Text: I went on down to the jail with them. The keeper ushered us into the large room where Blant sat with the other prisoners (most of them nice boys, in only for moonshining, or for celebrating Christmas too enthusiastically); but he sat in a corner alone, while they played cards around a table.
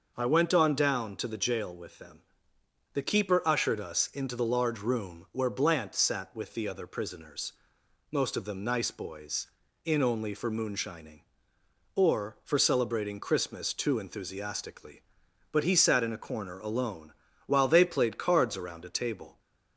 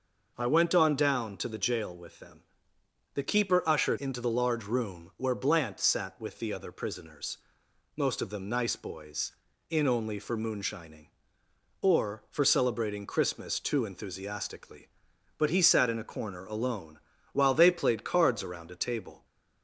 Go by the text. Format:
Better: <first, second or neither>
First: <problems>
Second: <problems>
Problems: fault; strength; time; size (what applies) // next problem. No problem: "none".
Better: first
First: none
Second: skips "us"; at 3.9 s